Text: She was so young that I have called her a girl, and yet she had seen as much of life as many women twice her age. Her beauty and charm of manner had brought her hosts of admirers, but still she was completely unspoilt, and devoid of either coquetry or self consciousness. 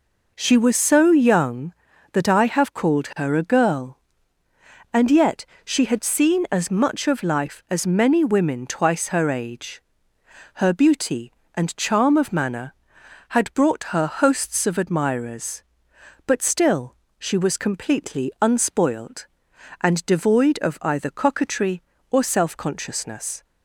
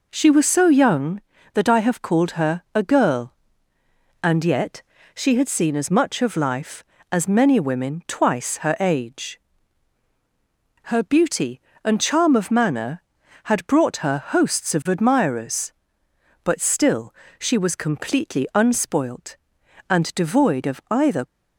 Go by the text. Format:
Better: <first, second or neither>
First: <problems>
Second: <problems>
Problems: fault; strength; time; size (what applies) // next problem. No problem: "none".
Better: first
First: pauses between "yet" and "she"; slight; at 5.4 s; 0.18 s long // pauses between "still" and "she"; slight; at 16.9 s; 0.24 s long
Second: pauses between "yet" and "she"; slight; at 4.8 s; 0.32 s long // pauses between "still" and "she"; slight; at 17.1 s; 0.24 s long // stops before "coquetry or self consciousness"; at 21.2 s